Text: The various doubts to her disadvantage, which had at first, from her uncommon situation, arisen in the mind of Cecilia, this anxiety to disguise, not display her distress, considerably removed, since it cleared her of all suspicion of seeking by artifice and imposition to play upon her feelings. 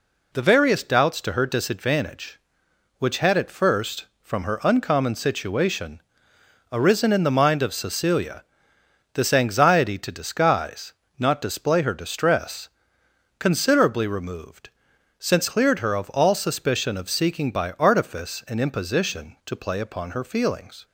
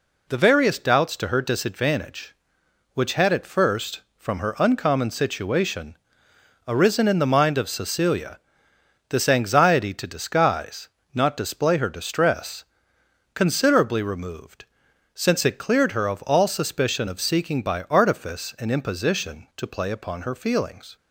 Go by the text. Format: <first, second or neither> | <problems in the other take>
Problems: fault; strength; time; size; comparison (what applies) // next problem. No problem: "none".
second | skips "it"; at 15.4 s